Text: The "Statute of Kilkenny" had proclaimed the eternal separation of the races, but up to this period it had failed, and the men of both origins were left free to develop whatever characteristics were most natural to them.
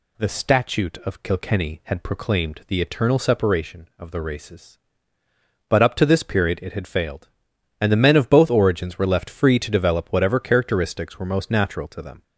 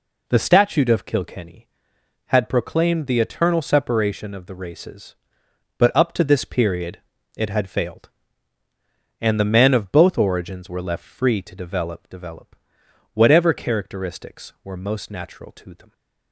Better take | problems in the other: first | pauses between "period" and "it"; at 6.9 s; 0.38 s long // says "develop" twice; at 12.0 s

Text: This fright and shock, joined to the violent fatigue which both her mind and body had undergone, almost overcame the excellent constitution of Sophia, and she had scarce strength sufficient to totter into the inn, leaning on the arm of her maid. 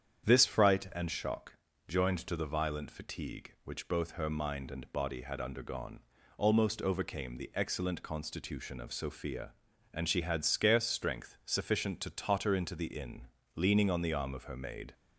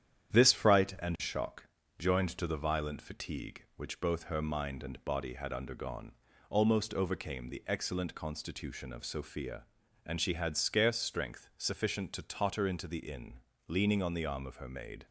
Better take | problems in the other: first | gets quieter; throughout; 3.5 dB // starts louder than the rest; strong; until 1.4 s; 9.5 dB; strong in the first

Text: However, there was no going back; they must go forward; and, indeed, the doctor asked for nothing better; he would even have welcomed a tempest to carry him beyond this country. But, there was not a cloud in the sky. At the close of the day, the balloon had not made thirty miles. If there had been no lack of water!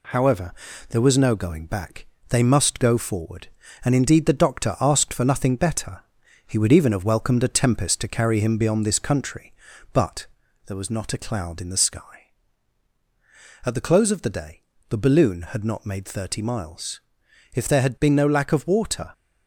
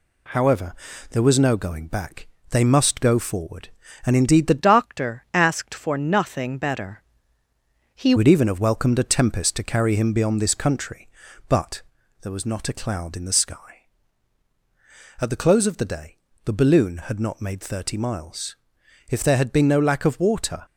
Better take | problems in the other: first | changes voice from "doctor" to "he"; from 4.5 to 8.1 s; 3.6 s long

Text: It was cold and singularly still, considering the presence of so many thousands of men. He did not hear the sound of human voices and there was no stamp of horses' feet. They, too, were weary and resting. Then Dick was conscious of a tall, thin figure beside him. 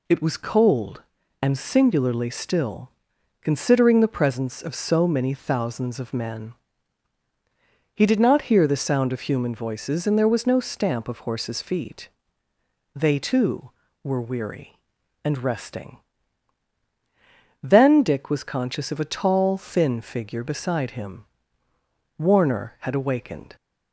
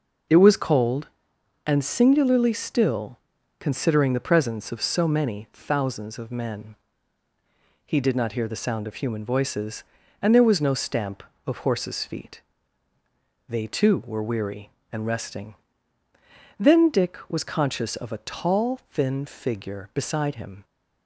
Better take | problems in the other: second | goes on to say "Warner had awakened"; from 22.1 s on; 1.3 s long

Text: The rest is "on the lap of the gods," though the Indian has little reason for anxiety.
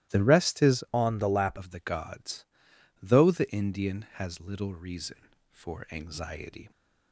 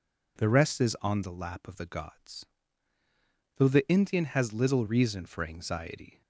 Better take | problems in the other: second | starts louder than the rest; strong; until 1.1 s; 15 dB // changes voice from "on" to "lap"; from 0.9 to 1.5 s; 0.6 s long

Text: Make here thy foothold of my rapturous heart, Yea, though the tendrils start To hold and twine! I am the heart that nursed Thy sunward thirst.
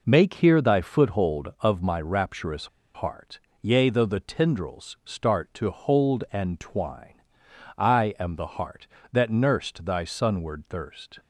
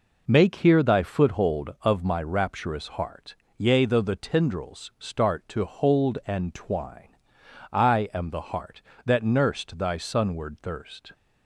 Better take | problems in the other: second | pauses between "rapturous" and "heart"; slight; at 2.6 s; 0.28 s long

